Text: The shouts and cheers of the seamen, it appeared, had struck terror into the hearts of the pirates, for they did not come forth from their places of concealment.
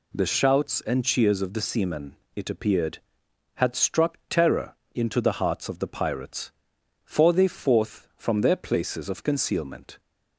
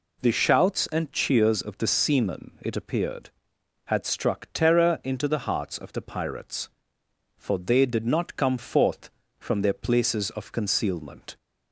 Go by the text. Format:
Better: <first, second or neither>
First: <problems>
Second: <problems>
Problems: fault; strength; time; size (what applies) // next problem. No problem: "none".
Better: second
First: pauses between "terror" and "into"; slight; at 4.7 s; 0.20 s long // skips "did not come"; at 7.4 s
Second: none